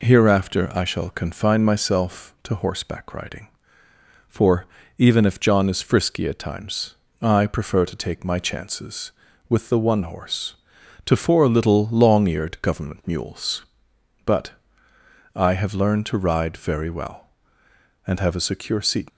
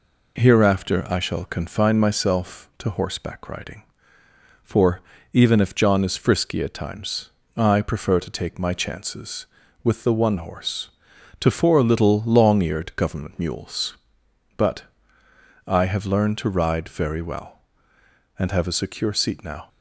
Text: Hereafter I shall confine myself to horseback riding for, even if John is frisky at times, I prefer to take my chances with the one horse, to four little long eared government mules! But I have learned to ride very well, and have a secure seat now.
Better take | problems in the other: second | pauses between "But" and "I"; noticeable; at 14.5 s; 0.84 s long; noticeable in the second // stops before "now"; at 19.0 s

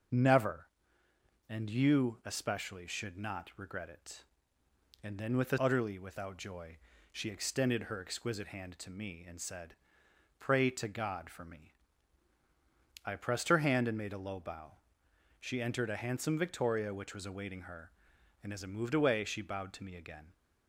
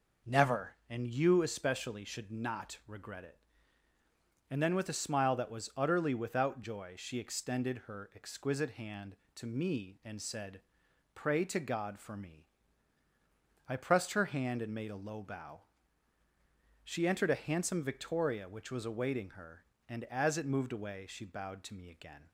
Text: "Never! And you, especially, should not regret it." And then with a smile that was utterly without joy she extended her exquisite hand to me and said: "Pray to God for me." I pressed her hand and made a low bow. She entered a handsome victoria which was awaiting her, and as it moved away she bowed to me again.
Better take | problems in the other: second | starts louder than the rest; noticeable; until 1.9 s; 6 dB // skips "smile that was"; at 5.5 s // pauses between "joy" and "she"; slight; at 6.7 s; 0.36 s long

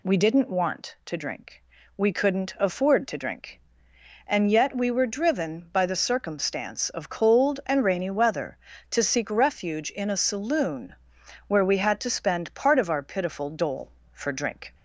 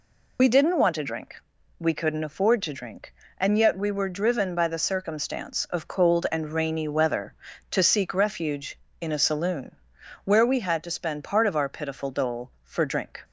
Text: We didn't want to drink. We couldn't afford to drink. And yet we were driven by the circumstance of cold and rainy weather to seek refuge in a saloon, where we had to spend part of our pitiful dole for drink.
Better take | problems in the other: first | loses the start of "We"; at 0.3 s; 40 ms

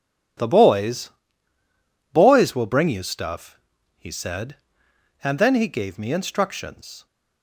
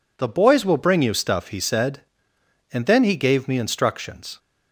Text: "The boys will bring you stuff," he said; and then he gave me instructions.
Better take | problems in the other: second | says "boys" twice; at 2.1 s

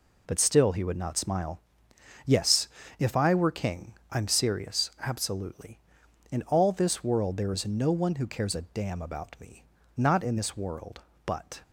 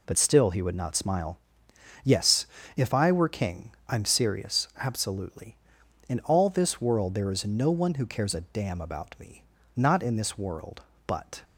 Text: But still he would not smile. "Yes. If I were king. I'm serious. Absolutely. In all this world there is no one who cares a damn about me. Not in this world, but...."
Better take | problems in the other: neither | none

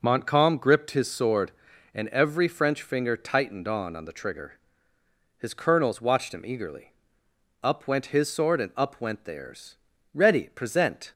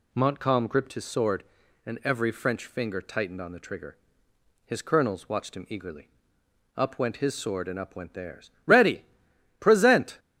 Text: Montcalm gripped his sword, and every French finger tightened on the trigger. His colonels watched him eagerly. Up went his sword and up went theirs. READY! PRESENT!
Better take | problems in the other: second | says "on" twice; at 3.9 s

